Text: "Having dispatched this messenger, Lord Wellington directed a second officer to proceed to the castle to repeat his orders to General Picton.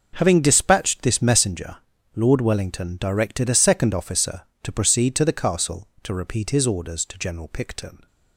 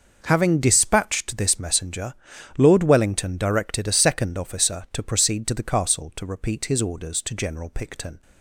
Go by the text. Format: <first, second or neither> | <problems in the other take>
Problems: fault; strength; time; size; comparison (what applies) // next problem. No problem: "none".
neither | none